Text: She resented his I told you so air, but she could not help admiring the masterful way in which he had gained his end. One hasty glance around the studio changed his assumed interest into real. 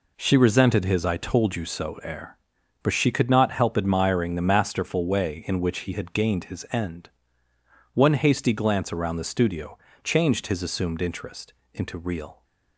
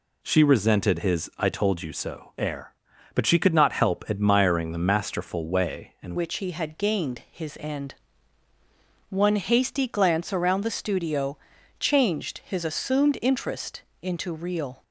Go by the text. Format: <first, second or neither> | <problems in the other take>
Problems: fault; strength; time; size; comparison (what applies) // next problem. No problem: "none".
first | changes voice at "which"; from 6.1 s on; 8.7 s long // pauses between "studio" and "changed"; at 11.3 s; 0.42 s long; slight in the first // pauses between "interest" and "into"; slight; at 13.8 s; 0.20 s long; slight in the first